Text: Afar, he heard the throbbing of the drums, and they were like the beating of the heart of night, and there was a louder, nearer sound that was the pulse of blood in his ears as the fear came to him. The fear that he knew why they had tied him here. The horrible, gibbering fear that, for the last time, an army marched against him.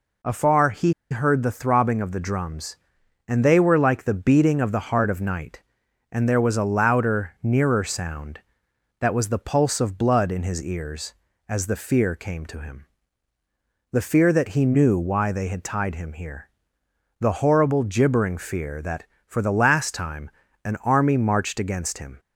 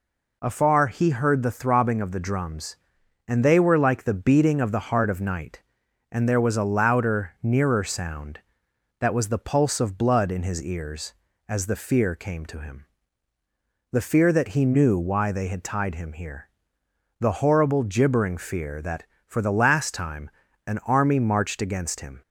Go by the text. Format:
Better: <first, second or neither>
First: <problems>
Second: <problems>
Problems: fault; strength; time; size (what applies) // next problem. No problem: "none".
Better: second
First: pauses between "he" and "heard"; slight; at 0.9 s; 0.18 s long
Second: none